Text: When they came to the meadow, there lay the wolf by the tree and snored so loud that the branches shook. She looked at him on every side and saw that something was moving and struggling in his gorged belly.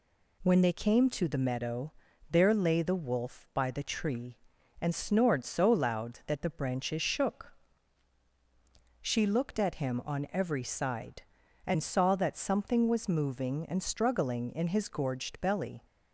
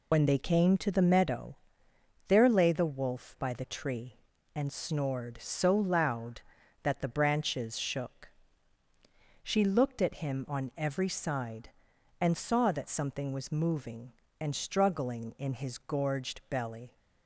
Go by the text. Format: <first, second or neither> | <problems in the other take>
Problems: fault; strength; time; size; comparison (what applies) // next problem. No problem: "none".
first | loses the start of "When"; at 0.1 s; 50 ms